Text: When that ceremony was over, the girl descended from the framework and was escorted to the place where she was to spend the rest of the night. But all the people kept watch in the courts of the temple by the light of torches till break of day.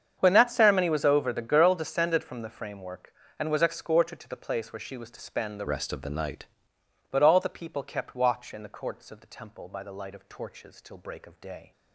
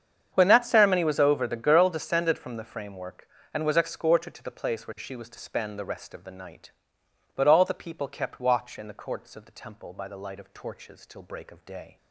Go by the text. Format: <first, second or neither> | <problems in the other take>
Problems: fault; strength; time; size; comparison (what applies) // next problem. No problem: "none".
second | starts louder than the rest; strong; until 1.2 s; 7.5 dB; strong in the second // changes voice from "rest" to "night"; from 5.6 to 6.4 s; 0.8 s long